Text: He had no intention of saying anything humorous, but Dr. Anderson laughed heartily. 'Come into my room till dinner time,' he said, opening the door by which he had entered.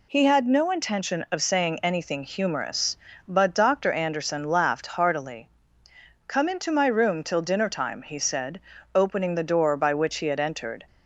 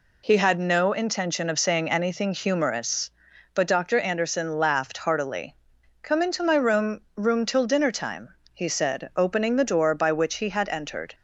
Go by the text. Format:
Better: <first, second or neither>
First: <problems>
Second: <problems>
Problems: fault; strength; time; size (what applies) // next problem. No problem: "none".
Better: first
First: none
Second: says "room" twice; at 7.1 s